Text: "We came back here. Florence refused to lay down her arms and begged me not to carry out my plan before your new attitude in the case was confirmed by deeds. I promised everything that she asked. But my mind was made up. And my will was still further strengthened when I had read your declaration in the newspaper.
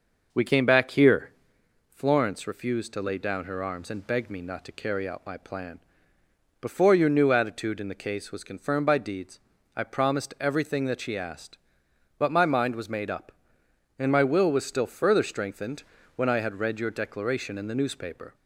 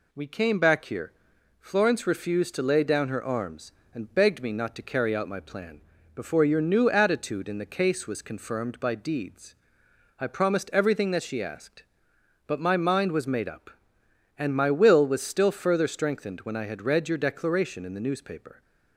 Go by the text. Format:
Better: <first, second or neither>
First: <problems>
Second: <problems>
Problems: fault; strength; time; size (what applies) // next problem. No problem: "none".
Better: second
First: starts louder than the rest; noticeable; until 1.6 s; 6 dB // pauses between "plan" and "before"; noticeable; at 5.8 s; 0.80 s long // pauses between "strengthened" and "when"; slight; at 15.8 s; 0.34 s long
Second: pauses between "plan" and "before"; slight; at 5.8 s; 0.34 s long